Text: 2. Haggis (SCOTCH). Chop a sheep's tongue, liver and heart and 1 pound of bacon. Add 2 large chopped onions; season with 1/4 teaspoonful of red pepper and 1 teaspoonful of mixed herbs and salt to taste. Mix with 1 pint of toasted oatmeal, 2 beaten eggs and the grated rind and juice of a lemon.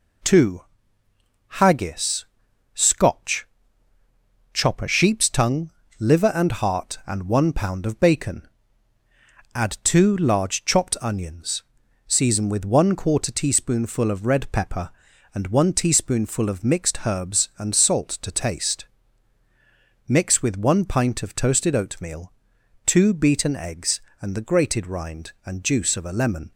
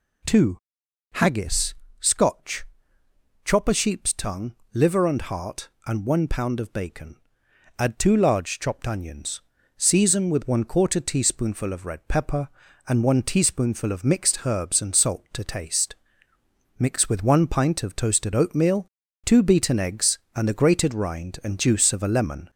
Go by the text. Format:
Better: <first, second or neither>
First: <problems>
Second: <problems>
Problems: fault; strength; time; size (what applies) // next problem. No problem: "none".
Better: first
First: none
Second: gets louder; slight; throughout; 2.5 dB